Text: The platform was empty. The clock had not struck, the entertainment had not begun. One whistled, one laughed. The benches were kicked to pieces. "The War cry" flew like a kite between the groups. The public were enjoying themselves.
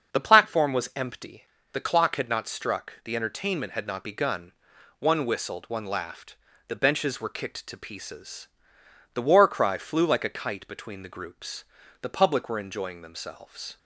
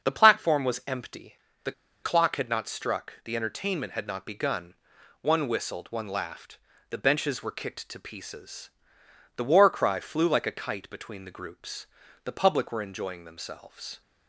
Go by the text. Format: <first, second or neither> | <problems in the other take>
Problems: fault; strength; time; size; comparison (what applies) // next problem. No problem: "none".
first | starts louder than the rest; until 1.1 s; 6.5 dB; also in the first // pauses between "The" and "clock"; slight; at 1.7 s; 0.31 s long